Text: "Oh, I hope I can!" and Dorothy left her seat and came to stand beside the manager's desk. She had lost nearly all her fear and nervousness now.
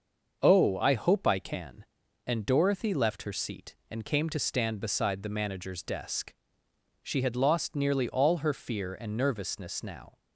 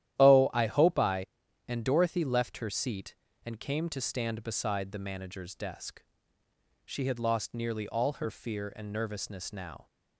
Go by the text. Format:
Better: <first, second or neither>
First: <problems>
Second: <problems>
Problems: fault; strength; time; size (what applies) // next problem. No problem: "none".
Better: first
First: starts louder than the rest; until 1.4 s; 6 dB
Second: starts louder than the rest; strong; until 1.2 s; 12 dB // skips "can"; at 1.4 s